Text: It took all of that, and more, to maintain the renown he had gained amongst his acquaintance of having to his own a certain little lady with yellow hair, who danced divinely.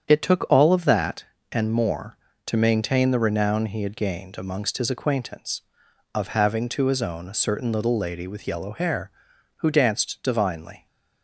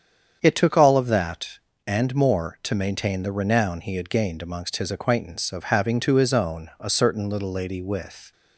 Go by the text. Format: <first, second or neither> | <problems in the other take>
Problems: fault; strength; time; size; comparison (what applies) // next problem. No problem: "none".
first | starts louder than the rest; strong; until 1.4 s; 7.5 dB; strong in the first // stops before "yellow hair who danced divinely"; at 8.3 s